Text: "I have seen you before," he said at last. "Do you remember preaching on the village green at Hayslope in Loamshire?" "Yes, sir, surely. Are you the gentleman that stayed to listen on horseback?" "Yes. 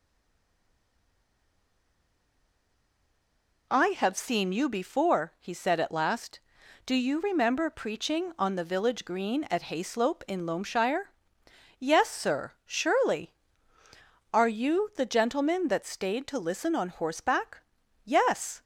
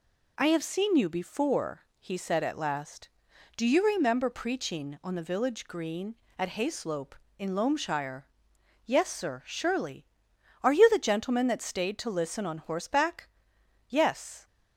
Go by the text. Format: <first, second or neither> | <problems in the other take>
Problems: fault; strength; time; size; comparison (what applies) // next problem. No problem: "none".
second | stays silent before the first word; strong; until 3.7 s; 3.7 s long